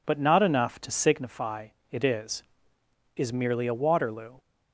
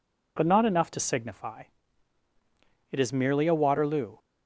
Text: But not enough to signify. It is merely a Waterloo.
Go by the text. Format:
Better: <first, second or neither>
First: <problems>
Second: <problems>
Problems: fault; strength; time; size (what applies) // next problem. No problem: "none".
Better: second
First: says "is" twice; at 3.1 s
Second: none